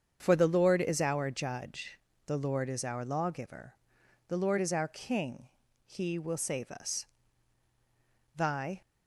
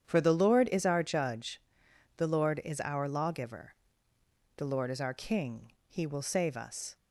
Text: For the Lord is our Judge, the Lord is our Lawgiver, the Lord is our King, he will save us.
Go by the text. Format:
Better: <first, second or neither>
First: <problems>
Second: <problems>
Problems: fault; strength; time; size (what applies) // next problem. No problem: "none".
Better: second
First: starts louder than the rest; strong; until 1.2 s; 7.5 dB // goes on to say "Thy"; slight; from 8.3 s on; 0.46 s long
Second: starts louder than the rest; strong; until 1.0 s; 8.5 dB